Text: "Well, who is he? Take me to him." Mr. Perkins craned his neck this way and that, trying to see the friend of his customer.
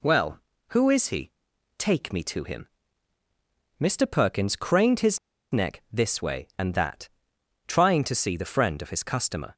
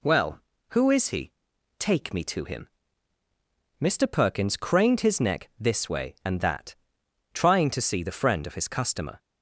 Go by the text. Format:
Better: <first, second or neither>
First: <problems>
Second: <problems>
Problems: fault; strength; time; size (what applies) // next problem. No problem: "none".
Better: second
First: pauses between "his" and "neck"; slight; at 5.1 s; 0.33 s long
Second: none